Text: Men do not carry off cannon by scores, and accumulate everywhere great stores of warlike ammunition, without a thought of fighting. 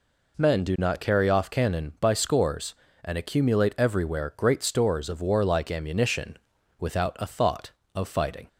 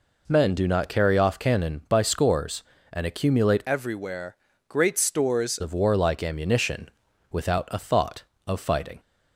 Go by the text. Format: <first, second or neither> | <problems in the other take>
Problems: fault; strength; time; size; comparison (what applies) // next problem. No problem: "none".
first | changes voice from "everywhere" to "stores"; from 3.6 to 5.5 s; 1.9 s long // pauses between "everywhere" and "great"; slight; at 4.3 s; 0.32 s long